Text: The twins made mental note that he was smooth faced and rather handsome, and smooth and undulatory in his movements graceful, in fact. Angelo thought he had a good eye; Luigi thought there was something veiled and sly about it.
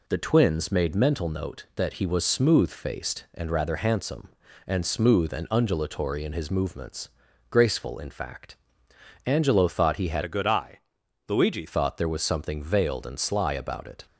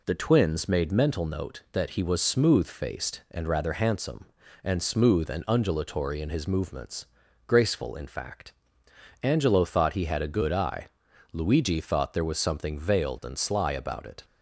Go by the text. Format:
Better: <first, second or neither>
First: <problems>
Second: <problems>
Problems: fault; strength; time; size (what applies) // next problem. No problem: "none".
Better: second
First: pauses between "movements" and "graceful"; at 7.0 s; 0.40 s long // changes voice from "a" to "Luigi"; from 10.2 to 11.6 s; 1.4 s long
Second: pauses between "movements" and "graceful"; at 7.0 s; 0.40 s long